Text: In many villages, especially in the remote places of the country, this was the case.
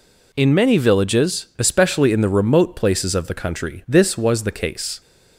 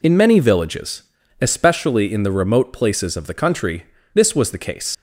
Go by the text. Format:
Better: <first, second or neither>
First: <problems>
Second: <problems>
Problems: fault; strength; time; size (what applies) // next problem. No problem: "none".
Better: first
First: none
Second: leaves "case" unfinished; at 4.9 s; 80 ms